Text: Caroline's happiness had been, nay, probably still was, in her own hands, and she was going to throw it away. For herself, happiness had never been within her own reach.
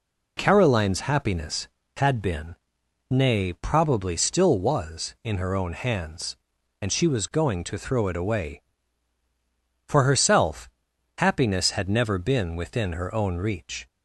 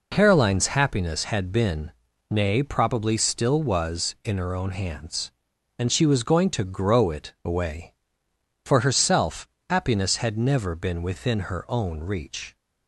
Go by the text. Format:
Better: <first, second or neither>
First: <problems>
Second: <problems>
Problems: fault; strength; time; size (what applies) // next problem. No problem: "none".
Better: first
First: none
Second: says "grow" for "throw"; at 6.6 s